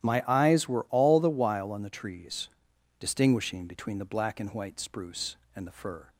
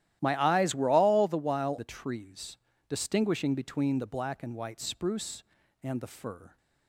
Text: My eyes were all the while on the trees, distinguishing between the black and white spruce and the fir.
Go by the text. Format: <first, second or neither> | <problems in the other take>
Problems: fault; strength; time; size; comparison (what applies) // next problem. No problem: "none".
first | starts louder than the rest; strong; until 1.2 s; 13 dB; strong in the first // skips "on"; at 1.7 s